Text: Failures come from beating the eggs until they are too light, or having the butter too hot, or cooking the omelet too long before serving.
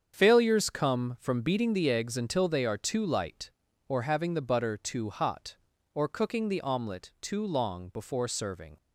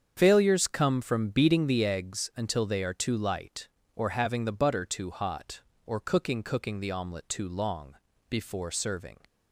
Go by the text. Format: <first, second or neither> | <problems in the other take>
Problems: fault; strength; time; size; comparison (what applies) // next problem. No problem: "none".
first | starts louder than the rest; until 1.2 s; 7 dB; strong in the first // says "cooking" twice; at 6.4 s // pauses between "long" and "before"; slight; at 7.9 s; 0.34 s long